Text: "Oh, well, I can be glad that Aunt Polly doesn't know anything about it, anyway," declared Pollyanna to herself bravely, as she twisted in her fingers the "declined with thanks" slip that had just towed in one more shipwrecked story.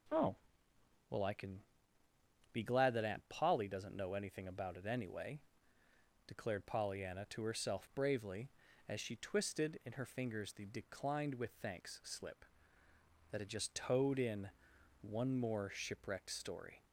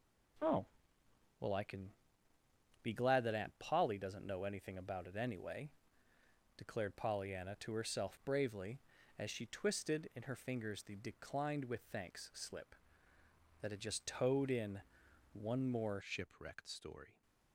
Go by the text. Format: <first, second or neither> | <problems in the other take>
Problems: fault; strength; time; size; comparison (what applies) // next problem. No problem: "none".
first | pauses between "can" and "be"; noticeable; at 1.9 s; 0.92 s long; noticeable in the first // pauses between "in" and "one"; noticeable; at 14.8 s; 0.50 s long; noticeable in the first // changes voice at "shipwrecked"; from 16.0 s on; 1.2 s long